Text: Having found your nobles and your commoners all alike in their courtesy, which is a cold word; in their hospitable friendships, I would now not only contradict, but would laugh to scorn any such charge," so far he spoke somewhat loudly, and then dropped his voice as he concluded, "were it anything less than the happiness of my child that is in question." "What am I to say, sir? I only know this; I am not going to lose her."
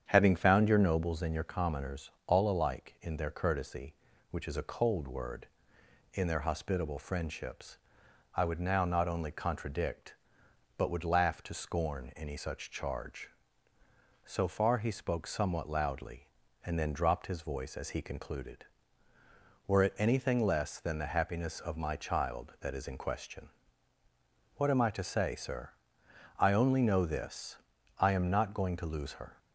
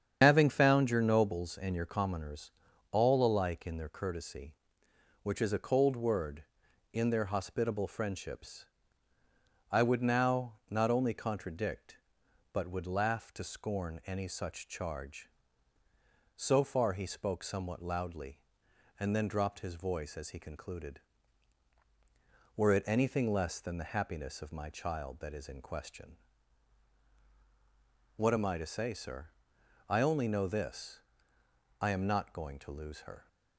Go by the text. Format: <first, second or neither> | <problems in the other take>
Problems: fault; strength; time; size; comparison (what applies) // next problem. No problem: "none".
first | loses the start of "Having"; at 0.2 s; 40 ms // starts louder than the rest; strong; until 1.2 s; 8 dB; strong in the first // pauses between "commoners" and "all"; at 2.5 s; 0.40 s long; slight in the first // pauses between "now" and "not"; slight; at 10.5 s; 0.16 s long